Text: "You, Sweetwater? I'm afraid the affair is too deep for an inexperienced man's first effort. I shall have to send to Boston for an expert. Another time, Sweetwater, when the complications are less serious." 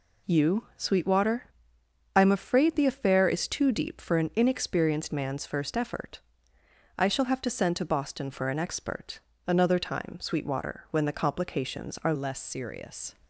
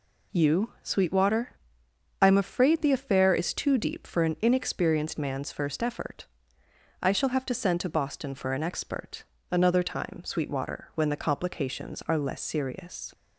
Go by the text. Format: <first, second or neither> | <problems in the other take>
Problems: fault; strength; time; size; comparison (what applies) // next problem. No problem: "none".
second | changes voice at "less"; from 12.1 s on; 1.0 s long